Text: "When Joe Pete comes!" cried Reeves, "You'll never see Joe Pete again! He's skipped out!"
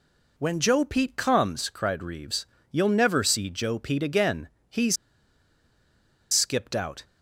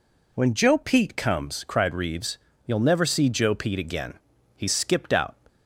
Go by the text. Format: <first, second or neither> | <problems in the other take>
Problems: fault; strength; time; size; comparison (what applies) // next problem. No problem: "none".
second | pauses between "He's" and "skipped"; strong; at 4.9 s; 1.3 s long